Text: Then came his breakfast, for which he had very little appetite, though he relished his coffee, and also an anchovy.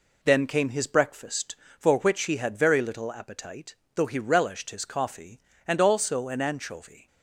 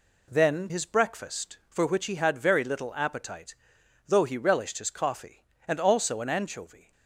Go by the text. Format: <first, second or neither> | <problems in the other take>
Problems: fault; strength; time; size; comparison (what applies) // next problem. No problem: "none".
first | skips "came"; at 0.6 s